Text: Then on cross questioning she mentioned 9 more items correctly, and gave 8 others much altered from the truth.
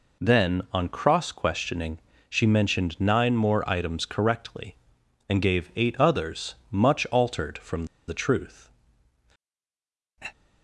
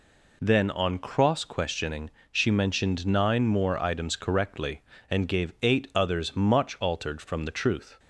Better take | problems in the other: second | pauses between "questioning" and "she"; slight; at 1.9 s; 0.32 s long; slight in the second // pauses between "others" and "much"; slight; at 6.5 s; 0.16 s long // pauses between "from" and "the"; slight; at 7.8 s; 0.23 s long

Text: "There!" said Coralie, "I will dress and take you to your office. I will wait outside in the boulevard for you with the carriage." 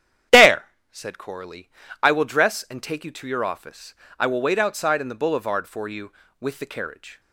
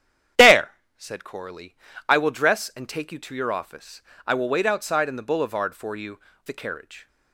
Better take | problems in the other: first | starts louder than the rest; strong; until 1.6 s; 10 dB; strong in the first // skips "with"; at 6.3 s

